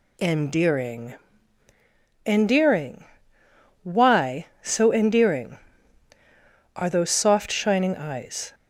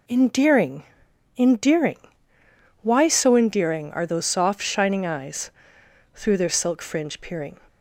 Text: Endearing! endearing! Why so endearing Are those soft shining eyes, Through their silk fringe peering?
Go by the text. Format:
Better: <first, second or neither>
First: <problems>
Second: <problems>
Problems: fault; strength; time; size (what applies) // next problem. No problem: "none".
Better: second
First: stops before "Through their silk fringe peering"; at 8.5 s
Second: none